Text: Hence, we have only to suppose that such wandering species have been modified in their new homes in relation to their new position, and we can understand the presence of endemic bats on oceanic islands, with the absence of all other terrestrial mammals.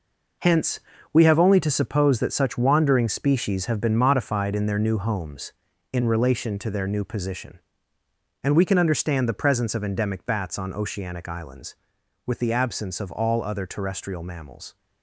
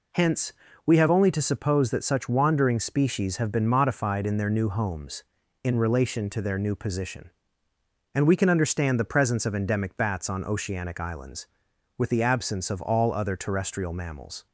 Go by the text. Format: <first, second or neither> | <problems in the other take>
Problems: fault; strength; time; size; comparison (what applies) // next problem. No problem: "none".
second | gets quieter; strong; throughout; 9.5 dB